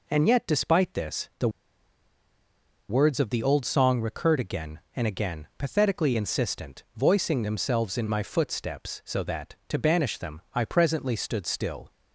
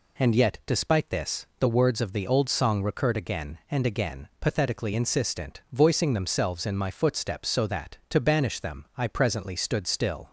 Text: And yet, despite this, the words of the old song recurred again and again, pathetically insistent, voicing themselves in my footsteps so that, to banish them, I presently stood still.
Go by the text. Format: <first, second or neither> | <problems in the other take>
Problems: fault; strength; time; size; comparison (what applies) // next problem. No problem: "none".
second | pauses between "the" and "words"; strong; at 1.4 s; 1.4 s long